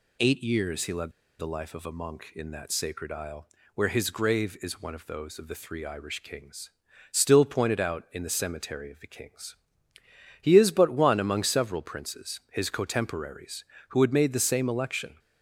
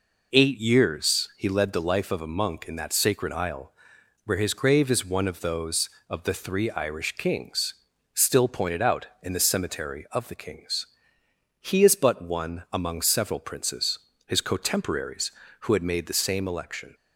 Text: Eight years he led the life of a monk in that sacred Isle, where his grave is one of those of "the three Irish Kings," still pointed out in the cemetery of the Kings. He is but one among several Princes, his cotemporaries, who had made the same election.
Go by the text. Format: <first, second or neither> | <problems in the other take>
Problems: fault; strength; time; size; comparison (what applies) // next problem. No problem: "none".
second | pauses between "led" and "the"; slight; at 1.1 s; 0.28 s long